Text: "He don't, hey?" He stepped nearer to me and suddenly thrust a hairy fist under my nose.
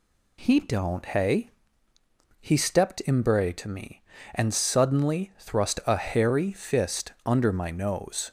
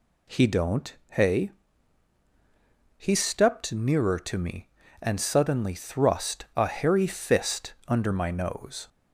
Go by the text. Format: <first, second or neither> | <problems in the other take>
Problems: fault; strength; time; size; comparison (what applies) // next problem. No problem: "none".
second | says "imbre" for "nearer"; at 3.0 s